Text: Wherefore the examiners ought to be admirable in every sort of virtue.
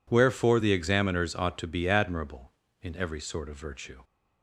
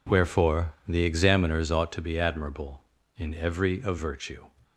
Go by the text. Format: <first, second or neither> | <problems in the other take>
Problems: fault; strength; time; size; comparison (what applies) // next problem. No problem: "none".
first | pauses between "Wherefore" and "the"; slight; at 0.7 s; 0.16 s long // skips "sort"; at 3.8 s